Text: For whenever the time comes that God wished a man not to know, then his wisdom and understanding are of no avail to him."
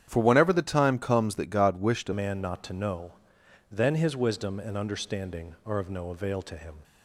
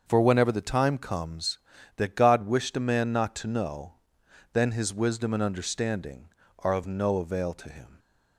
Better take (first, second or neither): second